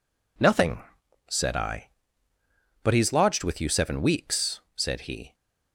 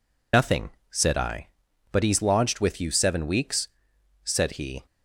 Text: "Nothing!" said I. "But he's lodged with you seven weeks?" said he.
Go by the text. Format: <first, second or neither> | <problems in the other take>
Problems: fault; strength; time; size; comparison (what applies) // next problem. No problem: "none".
first | loses the start of "Nothing"; at 0.3 s; 80 ms